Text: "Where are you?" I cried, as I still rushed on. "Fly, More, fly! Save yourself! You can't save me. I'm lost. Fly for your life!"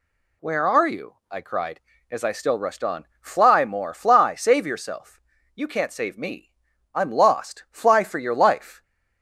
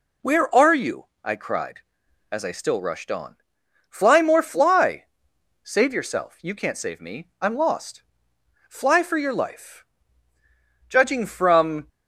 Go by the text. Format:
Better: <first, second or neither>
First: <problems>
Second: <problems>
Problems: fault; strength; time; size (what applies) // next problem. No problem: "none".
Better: first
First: none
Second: goes on to say "Judging from"; noticeable; from 10.8 s on; 0.98 s long